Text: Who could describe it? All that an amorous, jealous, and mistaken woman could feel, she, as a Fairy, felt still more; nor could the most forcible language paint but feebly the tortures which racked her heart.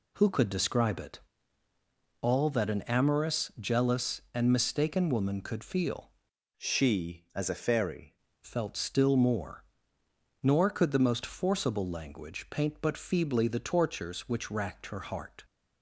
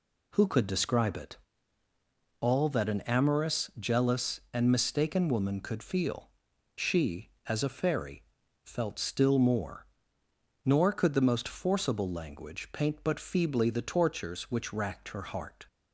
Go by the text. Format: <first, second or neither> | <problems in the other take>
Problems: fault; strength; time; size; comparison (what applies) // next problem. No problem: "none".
second | changes voice from "she" to "Fairy"; from 6.5 to 8.1 s; 1.6 s long